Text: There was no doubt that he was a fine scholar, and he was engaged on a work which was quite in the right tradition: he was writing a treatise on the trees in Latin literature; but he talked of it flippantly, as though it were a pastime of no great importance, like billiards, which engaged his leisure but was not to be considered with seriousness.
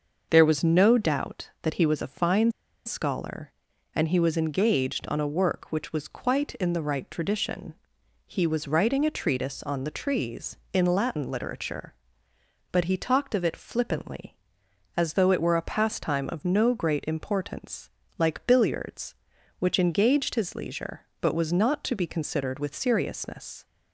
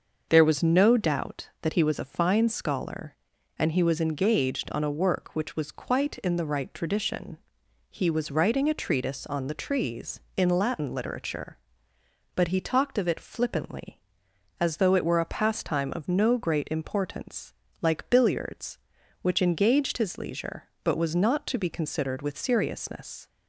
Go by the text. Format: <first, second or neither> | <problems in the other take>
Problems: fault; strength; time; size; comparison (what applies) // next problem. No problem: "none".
second | starts louder than the rest; until 1.3 s; 6 dB; also in the second // pauses between "fine" and "scholar"; slight; at 2.5 s; 0.34 s long